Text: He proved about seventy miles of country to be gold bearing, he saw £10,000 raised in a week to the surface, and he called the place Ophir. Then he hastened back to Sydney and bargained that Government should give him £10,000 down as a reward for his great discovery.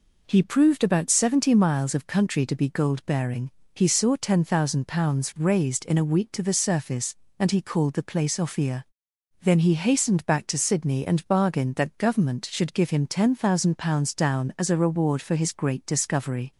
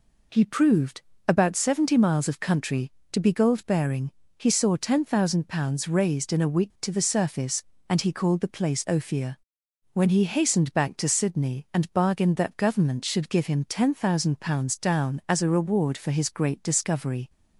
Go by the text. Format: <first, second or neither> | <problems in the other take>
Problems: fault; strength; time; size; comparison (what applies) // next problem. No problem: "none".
first | pauses between "proved" and "about"; slight; at 1.0 s; 0.26 s long // says "When" for "Then"; at 9.9 s